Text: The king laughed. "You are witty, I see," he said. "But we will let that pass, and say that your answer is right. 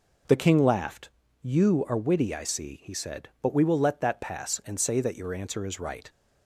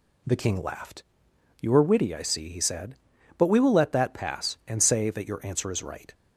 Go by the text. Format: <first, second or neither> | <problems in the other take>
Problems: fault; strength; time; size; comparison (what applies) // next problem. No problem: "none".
neither | none